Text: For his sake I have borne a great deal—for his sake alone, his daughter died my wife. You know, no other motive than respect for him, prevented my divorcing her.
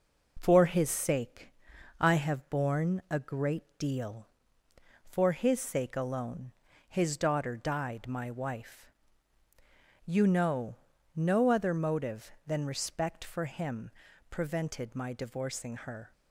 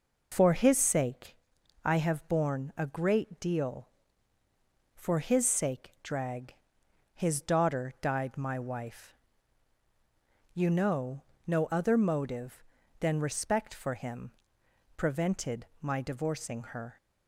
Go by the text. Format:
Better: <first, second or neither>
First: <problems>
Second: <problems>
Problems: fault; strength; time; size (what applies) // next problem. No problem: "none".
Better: first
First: pauses between "sake" and "I"; noticeable; at 1.5 s; 0.48 s long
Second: pauses between "sake" and "I"; noticeable; at 1.3 s; 0.48 s long // says "drag" for "alone"; at 6.0 s // pauses between "prevented" and "my"; slight; at 15.6 s; 0.16 s long